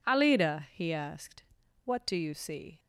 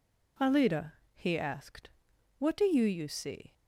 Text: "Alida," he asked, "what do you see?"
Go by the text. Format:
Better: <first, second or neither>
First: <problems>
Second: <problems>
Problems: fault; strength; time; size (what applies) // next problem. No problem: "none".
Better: first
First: none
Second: says "you" twice; at 2.8 s